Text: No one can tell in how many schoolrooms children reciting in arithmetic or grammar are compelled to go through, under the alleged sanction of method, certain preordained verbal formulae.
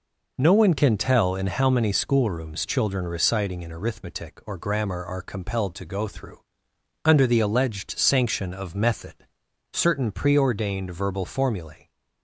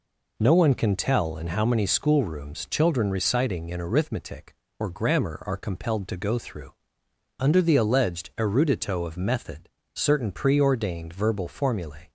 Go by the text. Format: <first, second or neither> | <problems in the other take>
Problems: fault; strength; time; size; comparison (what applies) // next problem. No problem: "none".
first | says "erudito" for "sanction"; at 8.3 s